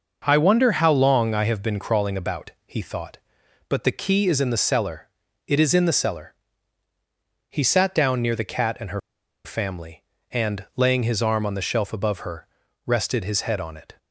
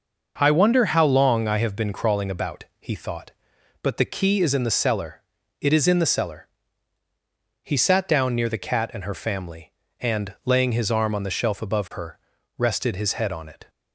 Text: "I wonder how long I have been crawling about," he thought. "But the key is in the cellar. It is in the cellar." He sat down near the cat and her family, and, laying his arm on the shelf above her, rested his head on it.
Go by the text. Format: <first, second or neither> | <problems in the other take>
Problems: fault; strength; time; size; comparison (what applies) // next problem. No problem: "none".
second | pauses between "her" and "family"; at 9.0 s; 0.45 s long